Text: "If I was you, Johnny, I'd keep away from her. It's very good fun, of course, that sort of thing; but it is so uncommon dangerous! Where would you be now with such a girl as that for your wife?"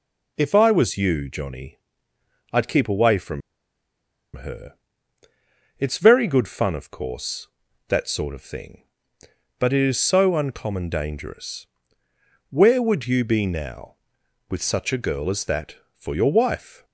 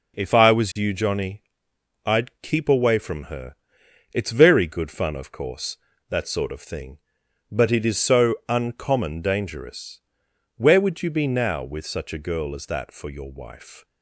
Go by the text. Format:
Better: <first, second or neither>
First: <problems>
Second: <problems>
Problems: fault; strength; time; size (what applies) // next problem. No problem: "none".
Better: second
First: pauses between "from" and "her"; noticeable; at 3.4 s; 0.95 s long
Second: none